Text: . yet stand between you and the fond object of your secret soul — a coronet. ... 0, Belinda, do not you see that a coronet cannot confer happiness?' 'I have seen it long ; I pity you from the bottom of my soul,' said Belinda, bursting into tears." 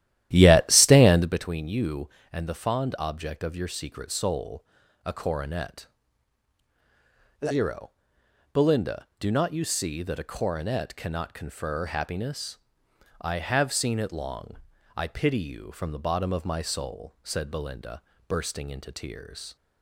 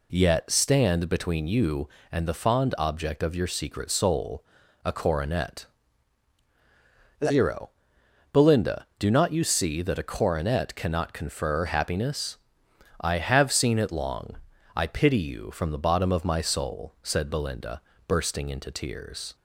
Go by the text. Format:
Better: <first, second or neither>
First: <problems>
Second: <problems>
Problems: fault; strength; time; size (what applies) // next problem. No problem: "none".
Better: second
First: starts louder than the rest; strong; until 1.4 s; 12.5 dB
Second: none